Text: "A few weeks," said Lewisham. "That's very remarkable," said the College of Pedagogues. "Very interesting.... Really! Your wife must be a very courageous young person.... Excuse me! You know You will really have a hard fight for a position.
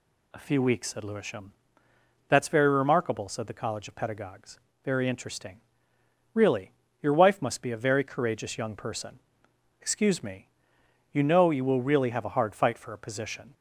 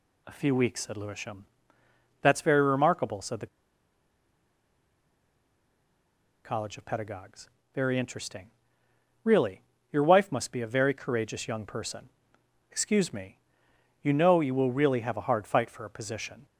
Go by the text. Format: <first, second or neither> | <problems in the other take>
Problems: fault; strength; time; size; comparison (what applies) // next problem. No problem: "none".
first | pauses between "the" and "College"; strong; at 3.4 s; 2.9 s long